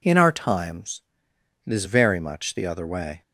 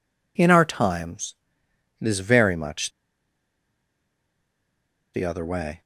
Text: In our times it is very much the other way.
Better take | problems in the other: first | pauses between "times" and "it"; noticeable; at 1.3 s; 0.64 s long; noticeable in the first // pauses between "much" and "the"; strong; at 2.9 s; 2.2 s long

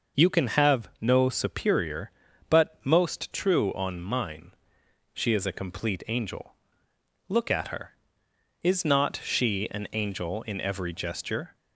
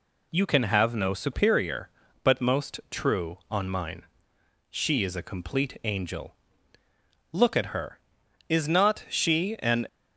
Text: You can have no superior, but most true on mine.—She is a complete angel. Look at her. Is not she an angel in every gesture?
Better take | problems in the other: first | stops before "angel in every gesture"; at 9.8 s

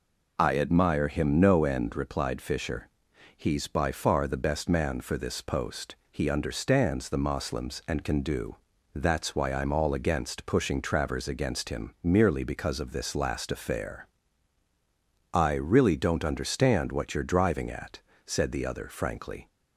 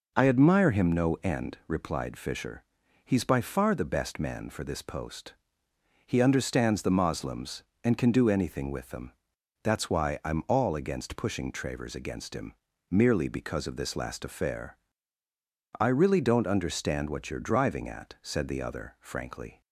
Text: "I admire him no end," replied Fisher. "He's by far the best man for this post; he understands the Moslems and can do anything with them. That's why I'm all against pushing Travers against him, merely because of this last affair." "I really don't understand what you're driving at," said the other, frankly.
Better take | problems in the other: second | skips "anything with them"; at 8.7 s

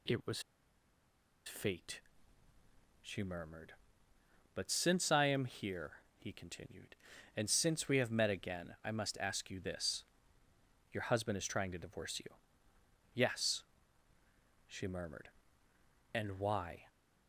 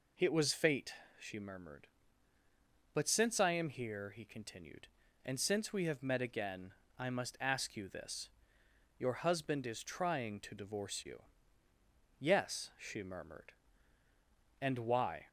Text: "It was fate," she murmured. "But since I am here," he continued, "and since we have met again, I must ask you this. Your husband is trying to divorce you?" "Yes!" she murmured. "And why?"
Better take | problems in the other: second | pauses between "was" and "fate"; at 0.4 s; 1.0 s long

